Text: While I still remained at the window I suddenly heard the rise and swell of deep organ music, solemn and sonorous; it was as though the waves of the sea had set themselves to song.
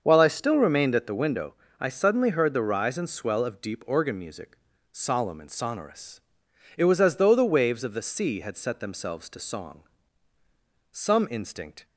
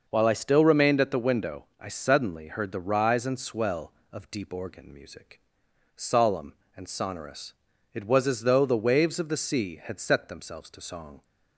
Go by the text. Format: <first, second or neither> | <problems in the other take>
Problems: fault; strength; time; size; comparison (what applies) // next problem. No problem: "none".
second | starts louder than the rest; until 1.0 s; 6.5 dB // pauses between "window" and "I"; slight; at 1.5 s; 0.24 s long; slight in the second // goes on to say "Some instinct"; noticeable; from 10.9 s on; 0.94 s long